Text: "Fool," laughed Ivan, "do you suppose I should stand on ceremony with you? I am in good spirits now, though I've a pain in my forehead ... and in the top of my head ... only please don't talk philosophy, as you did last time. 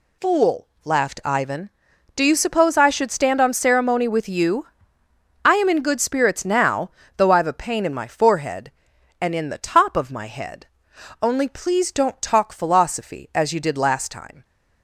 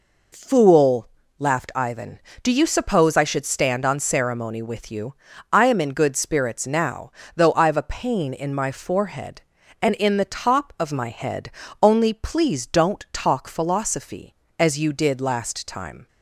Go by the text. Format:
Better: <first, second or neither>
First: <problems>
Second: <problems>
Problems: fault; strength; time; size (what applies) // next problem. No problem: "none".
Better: neither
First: none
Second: none